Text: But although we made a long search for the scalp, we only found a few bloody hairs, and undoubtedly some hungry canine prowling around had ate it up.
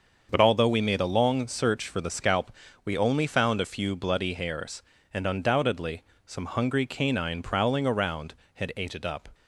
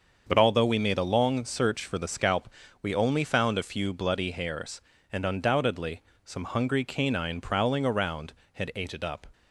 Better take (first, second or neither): neither